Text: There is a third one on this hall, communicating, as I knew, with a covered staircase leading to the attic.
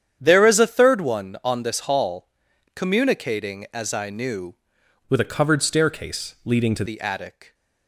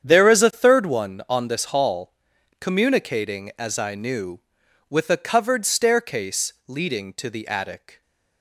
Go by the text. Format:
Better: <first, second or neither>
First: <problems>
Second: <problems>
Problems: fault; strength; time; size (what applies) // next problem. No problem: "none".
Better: second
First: starts louder than the rest; strong; until 1.2 s; 9 dB // changes voice from "with" to "to"; from 5.0 to 6.8 s; 1.8 s long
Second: starts louder than the rest; strong; until 1.0 s; 8.5 dB